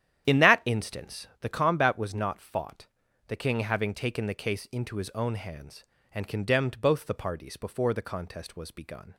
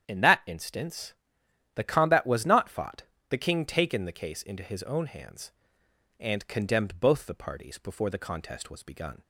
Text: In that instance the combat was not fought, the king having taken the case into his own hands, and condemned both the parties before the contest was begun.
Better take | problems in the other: first | starts louder than the rest; strong; until 1.1 s; 9 dB; strong in the first // pauses between "instance" and "the"; noticeable; at 1.1 s; 0.62 s long // skips "having"; at 3.6 s

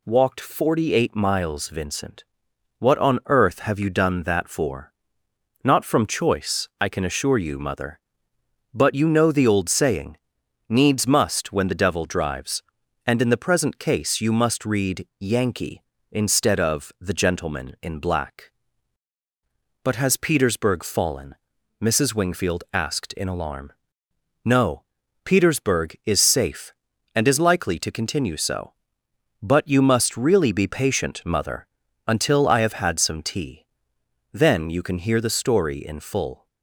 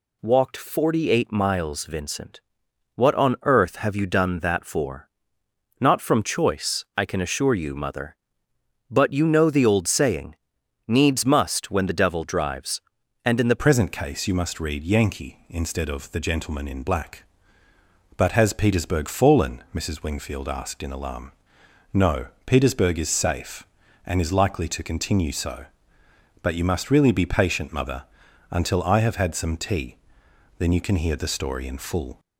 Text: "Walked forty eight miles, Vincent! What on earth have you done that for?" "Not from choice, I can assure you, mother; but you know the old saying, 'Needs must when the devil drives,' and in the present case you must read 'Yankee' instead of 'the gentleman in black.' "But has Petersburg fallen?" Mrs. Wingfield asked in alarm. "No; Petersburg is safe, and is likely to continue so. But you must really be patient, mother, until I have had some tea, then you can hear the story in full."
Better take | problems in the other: first | changes voice at "present"; from 13.6 s on; 18.5 s long

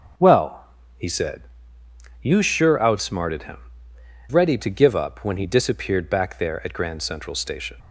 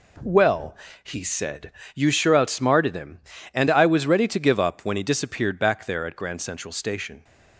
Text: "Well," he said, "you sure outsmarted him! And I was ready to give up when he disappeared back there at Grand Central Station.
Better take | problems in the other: second | starts louder than the rest; strong; until 2.3 s; 7 dB // skips "And I was"; at 3.9 s

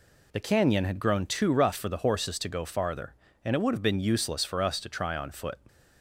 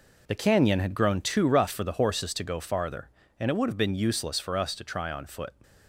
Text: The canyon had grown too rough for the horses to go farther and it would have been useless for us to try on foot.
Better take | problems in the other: first | gets quieter; strong; throughout; 7.5 dB

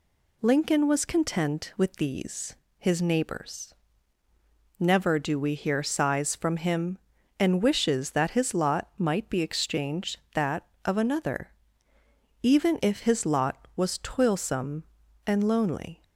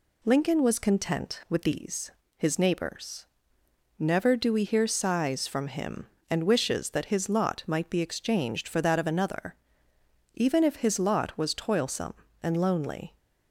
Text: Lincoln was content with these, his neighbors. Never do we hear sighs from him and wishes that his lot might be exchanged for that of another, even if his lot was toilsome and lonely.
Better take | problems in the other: second | skips "for"; at 10.2 s

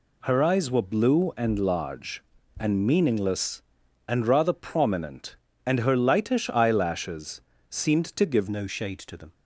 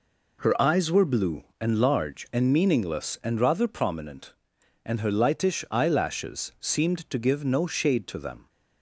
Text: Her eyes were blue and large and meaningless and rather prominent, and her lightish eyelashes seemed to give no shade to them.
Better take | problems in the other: second | pauses between "eyelashes" and "seemed"; slight; at 7.3 s; 0.30 s long // changes voice at "no"; from 8.4 s on; 0.9 s long

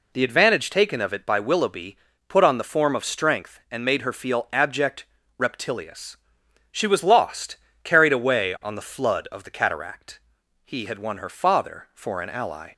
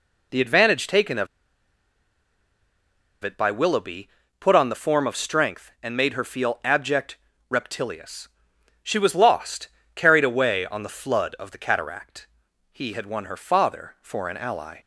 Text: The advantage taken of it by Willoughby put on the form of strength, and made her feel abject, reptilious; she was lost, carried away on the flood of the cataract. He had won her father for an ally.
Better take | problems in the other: first | pauses between "of" and "it"; strong; at 1.2 s; 1.9 s long // pauses between "Willoughby" and "put"; slight; at 4.0 s; 0.32 s long; slight in the first

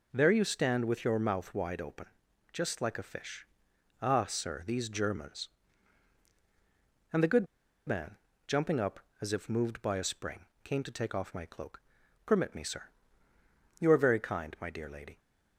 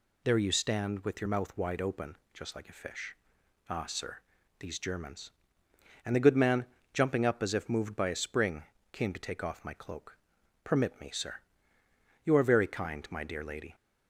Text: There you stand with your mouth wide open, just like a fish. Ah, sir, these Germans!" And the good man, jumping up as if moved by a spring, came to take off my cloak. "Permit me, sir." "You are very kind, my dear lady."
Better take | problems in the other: second | pauses between "good" and "man"; at 7.4 s; 0.40 s long

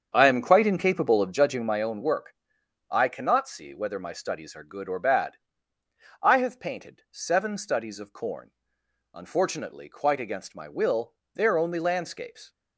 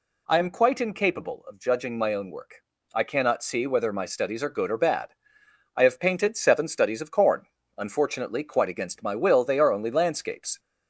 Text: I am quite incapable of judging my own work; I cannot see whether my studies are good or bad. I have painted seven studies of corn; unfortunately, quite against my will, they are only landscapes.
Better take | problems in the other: second | starts louder than the rest; strong; until 1.9 s; 7.5 dB

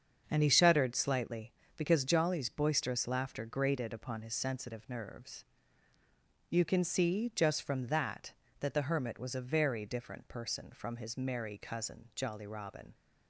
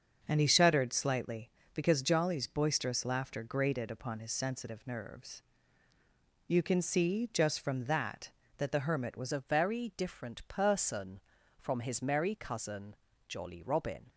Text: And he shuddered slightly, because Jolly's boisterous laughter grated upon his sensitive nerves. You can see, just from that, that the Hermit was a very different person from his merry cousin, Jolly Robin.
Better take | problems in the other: first | starts louder than the rest; until 1.2 s; 6.5 dB; also in the first // changes voice at "a"; from 9.3 s on; 4.7 s long

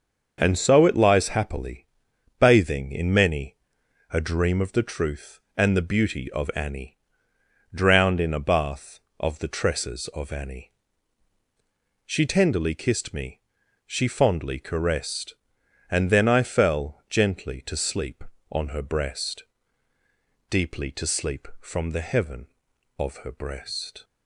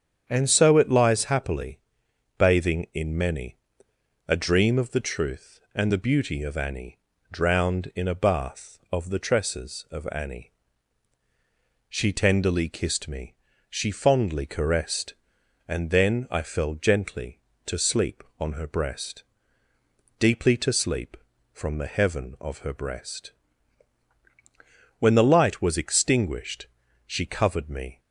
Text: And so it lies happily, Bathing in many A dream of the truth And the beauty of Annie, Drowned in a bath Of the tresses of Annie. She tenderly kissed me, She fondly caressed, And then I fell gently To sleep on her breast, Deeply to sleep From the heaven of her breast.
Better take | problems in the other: first | starts louder than the rest; strong; until 1.2 s; 8 dB; also in the first // pauses between "many" and "A"; noticeable; at 3.5 s; 0.70 s long; noticeable in the first // goes on to say "When the light was extinguished She covered me"; strong; from 24.9 s on; 3.0 s long

